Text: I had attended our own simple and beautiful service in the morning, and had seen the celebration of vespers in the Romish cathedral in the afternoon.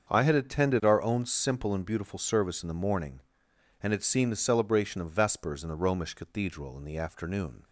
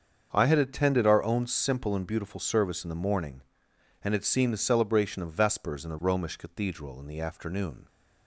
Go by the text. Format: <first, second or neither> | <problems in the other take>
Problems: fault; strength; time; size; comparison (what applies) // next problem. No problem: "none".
neither | starts louder than the rest; the same in both